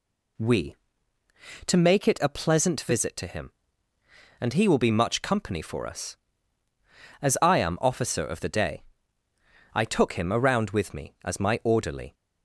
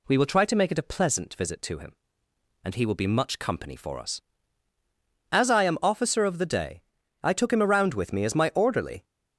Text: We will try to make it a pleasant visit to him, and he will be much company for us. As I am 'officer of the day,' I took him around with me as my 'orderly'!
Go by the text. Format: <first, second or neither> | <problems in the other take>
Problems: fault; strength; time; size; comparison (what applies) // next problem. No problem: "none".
second | skips "will try"; at 1.2 s